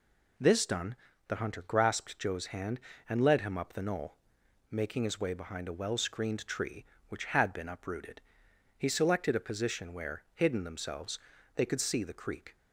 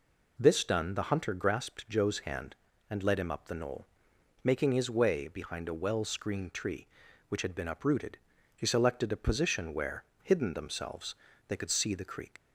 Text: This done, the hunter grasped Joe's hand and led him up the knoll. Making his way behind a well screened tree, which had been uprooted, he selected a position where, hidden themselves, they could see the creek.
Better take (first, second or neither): first